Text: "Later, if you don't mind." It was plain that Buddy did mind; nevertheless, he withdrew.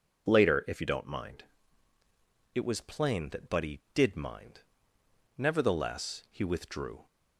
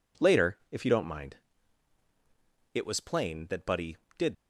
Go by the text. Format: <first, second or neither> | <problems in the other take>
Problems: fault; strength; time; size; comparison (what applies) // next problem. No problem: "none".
first | stops before "mind nevertheless he withdrew"; at 4.3 s